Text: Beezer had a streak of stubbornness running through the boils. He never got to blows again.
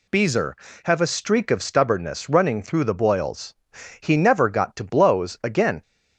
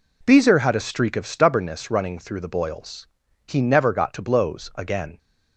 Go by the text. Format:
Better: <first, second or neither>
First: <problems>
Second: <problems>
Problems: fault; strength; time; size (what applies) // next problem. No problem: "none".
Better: second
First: says "have" for "had"; at 0.8 s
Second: none